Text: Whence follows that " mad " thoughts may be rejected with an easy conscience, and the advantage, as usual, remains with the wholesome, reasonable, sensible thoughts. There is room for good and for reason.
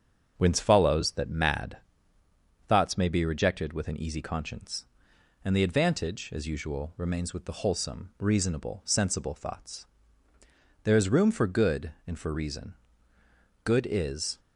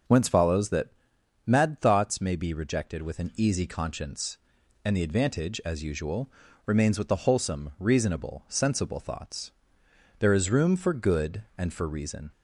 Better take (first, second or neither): second